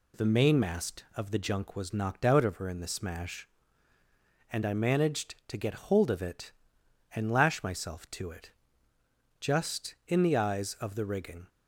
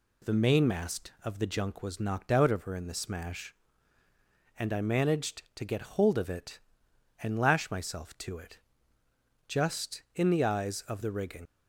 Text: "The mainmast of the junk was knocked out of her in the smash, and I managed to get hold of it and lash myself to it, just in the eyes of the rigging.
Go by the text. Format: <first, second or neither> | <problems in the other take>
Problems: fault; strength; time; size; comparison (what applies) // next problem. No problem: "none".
first | leaves "rigging" unfinished; at 11.4 s; 85 ms